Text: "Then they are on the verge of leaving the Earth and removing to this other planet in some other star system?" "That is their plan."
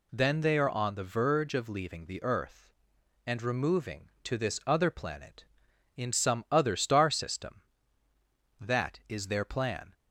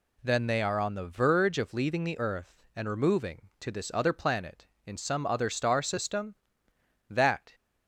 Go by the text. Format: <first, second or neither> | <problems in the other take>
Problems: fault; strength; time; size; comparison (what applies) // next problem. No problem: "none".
first | stops before "is their plan"; at 7.5 s